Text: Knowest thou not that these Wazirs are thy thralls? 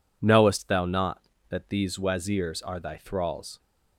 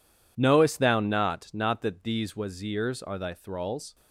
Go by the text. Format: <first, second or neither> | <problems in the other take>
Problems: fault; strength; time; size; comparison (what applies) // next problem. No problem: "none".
first | says "not" twice; at 1.5 s